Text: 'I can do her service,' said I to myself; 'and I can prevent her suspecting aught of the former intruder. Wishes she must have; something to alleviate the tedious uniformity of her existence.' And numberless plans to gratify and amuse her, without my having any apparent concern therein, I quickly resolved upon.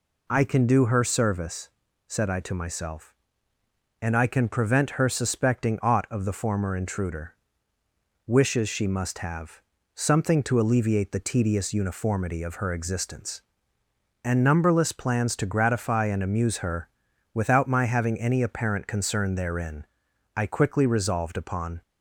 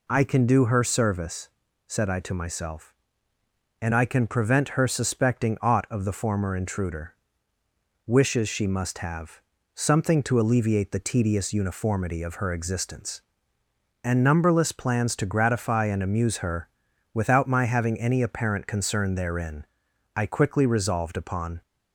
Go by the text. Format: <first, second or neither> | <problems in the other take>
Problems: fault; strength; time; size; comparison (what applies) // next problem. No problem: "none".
neither | none